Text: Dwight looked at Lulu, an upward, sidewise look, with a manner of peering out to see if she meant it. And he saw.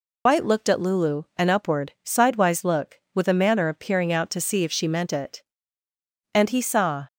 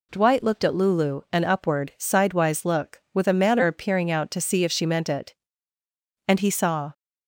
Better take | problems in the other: second | loses the start of "Dwight"; at 0.2 s; 115 ms

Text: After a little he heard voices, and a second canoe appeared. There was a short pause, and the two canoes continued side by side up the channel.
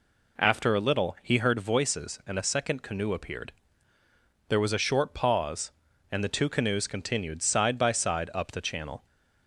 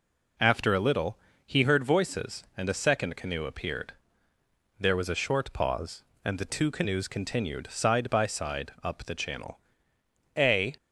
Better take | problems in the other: first | pauses between "little" and "he"; slight; at 1.1 s; 0.28 s long // goes on to say "A"; slight; from 10.3 s on; 0.40 s long

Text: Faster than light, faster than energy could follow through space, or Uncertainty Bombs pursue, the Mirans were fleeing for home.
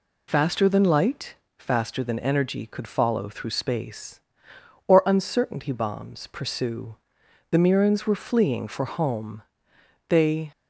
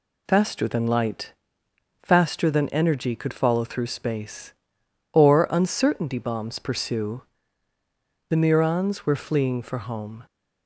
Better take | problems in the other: second | goes on to say "They"; slight; from 10.0 s on; 0.42 s long

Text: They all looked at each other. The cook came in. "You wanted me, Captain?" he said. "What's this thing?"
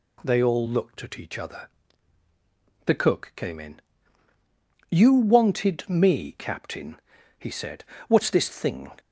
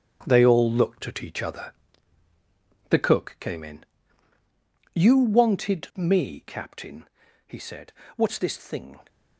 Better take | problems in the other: first | gets quieter; strong; throughout; 9 dB

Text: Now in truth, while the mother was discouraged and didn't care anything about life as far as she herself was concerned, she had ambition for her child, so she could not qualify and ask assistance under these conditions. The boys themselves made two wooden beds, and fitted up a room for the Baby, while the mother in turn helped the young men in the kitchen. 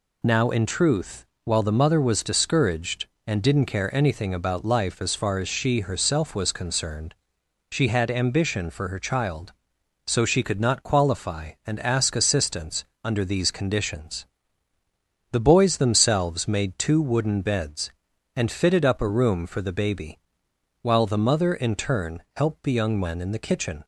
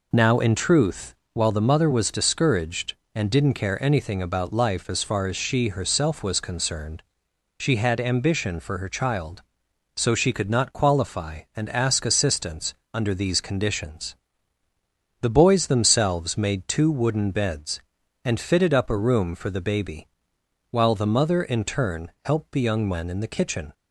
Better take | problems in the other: first | starts louder than the rest; noticeable; until 1.5 s; 4 dB // pauses between "assistance" and "under"; slight; at 12.7 s; 0.18 s long; slight in the first

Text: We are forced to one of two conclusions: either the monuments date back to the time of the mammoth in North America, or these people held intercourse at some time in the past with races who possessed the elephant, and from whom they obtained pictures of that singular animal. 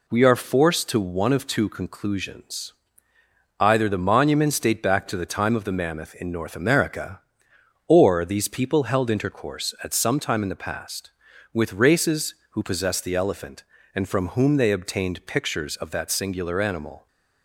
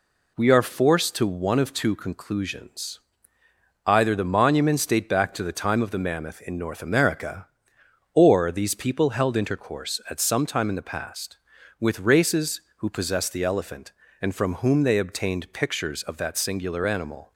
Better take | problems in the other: neither | none

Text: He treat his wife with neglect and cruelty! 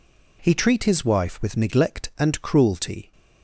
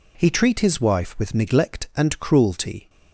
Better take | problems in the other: neither | none

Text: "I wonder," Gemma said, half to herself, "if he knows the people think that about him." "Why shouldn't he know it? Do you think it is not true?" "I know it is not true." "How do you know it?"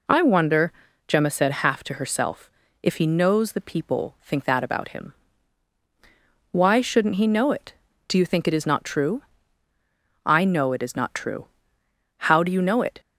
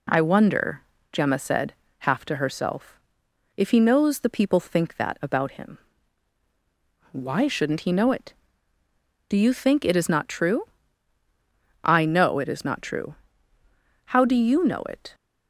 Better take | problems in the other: neither | none

